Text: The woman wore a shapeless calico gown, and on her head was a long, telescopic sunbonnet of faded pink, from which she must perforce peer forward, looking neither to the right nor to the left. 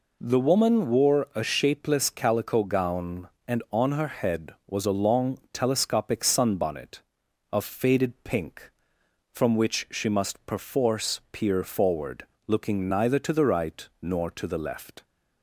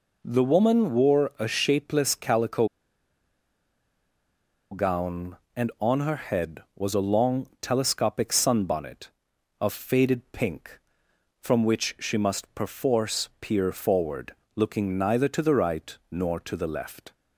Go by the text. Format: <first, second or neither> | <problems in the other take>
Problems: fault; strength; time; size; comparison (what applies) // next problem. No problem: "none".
first | pauses between "calico" and "gown"; strong; at 2.6 s; 2.0 s long